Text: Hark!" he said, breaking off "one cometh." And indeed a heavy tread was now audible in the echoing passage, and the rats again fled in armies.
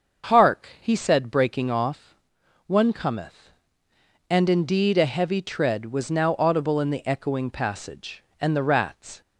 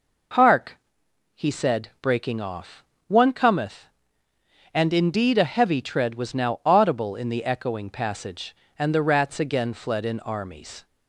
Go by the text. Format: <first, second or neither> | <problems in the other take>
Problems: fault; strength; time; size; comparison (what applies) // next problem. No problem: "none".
second | starts louder than the rest; until 1.4 s; 6.5 dB // pauses between "off" and "one"; noticeable; at 2.1 s; 0.50 s long; slight in the second // stops before "again fled in armies"; at 9.2 s